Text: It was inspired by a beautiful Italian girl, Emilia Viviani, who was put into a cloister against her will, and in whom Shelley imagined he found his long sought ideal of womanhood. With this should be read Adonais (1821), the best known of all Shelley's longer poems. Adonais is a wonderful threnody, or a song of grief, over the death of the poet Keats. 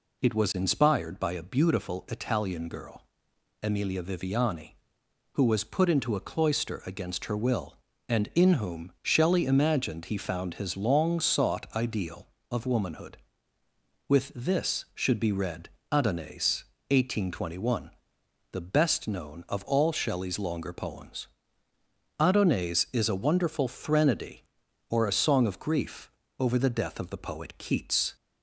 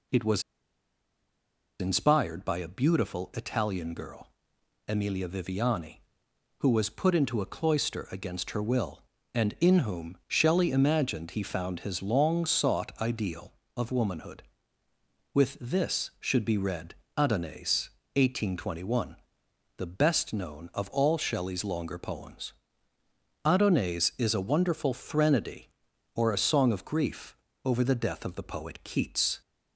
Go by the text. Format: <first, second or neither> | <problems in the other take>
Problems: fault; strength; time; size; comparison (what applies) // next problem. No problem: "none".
first | pauses between "was" and "inspired"; strong; at 0.4 s; 1.3 s long // pauses between "read" and "Adonais"; slight; at 16.9 s; 0.22 s long; slight in the first